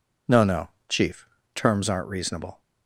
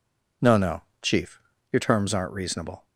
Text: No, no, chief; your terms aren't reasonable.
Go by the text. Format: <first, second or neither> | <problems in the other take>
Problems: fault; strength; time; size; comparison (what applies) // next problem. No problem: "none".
second | skips "your"; at 1.4 s